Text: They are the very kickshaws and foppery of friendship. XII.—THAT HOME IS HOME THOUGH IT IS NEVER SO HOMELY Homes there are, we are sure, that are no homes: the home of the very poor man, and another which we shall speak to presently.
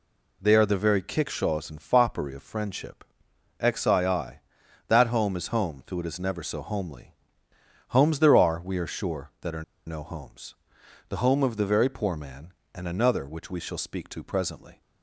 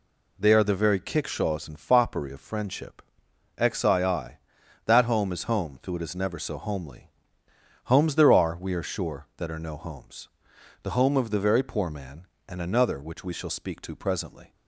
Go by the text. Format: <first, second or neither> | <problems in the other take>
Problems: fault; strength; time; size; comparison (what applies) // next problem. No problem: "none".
second | pauses between "HOMELY" and "Homes"; noticeable; at 7.1 s; 0.74 s long; noticeable in the second // pauses between "are" and "no"; slight; at 9.6 s; 0.24 s long